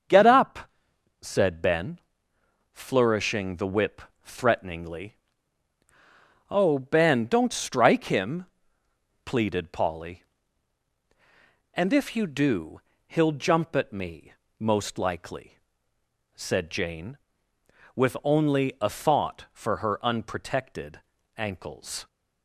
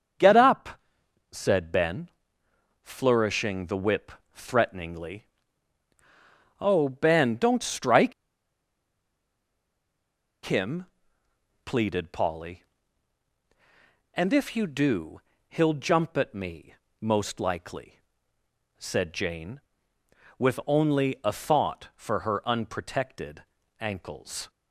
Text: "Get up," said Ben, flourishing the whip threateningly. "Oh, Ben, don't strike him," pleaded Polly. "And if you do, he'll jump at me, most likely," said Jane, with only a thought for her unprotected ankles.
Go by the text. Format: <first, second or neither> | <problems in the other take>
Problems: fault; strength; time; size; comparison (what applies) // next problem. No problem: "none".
first | starts louder than the rest; until 1.7 s; 7 dB; also in the first // pauses between "whip" and "threateningly"; slight; at 4.1 s; 0.20 s long; slight in the first // pauses between "strike" and "him"; strong; at 8.1 s; 2.3 s long // pauses between "unprotected" and "ankles"; at 23.4 s; 0.38 s long; also in the first